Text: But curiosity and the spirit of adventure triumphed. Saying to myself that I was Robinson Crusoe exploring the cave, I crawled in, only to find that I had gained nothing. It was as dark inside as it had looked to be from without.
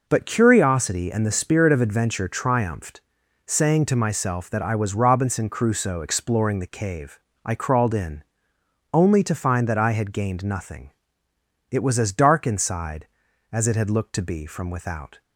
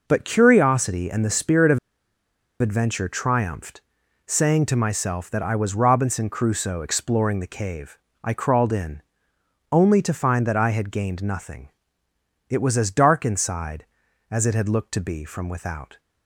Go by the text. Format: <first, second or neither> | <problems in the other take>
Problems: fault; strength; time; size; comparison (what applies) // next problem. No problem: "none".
first | pauses between "of" and "adventure"; noticeable; at 1.7 s; 0.82 s long